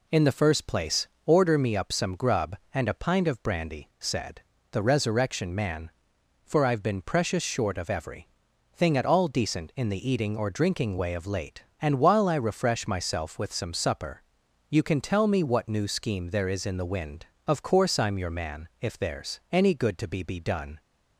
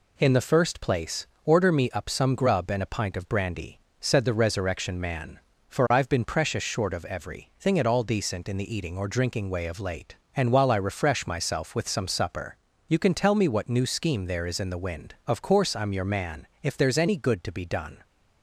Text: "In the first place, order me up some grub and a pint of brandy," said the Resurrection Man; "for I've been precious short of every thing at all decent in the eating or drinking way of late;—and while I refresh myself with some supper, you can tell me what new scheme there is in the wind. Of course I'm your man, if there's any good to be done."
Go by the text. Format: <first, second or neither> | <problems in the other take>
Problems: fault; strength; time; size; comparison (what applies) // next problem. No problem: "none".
second | pauses between "said" and "the"; slight; at 4.4 s; 0.30 s long // pauses between "every" and "thing"; at 8.2 s; 0.44 s long // says "be" twice; at 20.2 s